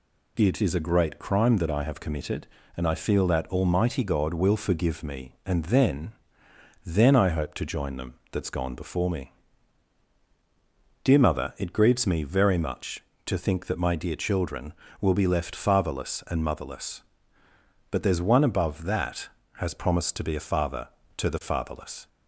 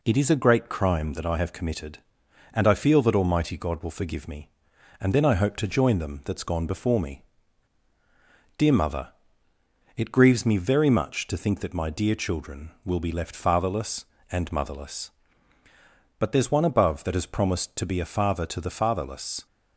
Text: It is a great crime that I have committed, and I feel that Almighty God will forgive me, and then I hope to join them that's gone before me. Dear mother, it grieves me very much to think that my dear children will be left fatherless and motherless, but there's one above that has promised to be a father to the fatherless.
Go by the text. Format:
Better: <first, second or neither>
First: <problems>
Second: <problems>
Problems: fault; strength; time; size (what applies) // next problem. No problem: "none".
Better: second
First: says "then" twice; at 6.8 s // pauses between "them" and "that's"; slight; at 8.1 s; 0.18 s long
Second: none